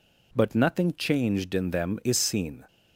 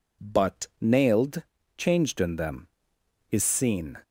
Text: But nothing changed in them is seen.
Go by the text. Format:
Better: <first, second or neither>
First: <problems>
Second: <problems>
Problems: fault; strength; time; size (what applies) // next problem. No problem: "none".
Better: first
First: none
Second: says "nailed" for "nothing"; at 0.8 s